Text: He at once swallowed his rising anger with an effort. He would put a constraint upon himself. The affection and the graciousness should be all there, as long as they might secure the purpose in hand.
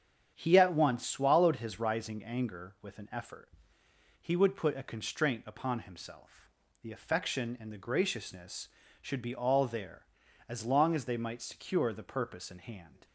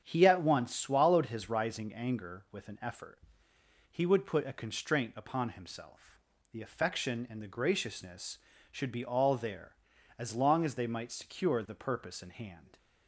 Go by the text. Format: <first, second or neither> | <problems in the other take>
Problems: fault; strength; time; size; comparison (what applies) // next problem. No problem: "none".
neither | starts louder than the rest; strong; the same in both